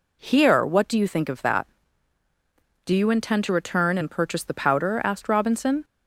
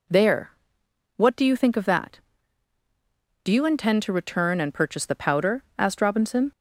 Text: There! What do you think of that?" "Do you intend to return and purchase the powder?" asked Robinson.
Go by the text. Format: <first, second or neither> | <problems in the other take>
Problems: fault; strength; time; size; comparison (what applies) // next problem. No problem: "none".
second | says "Here" for "There"; at 0.2 s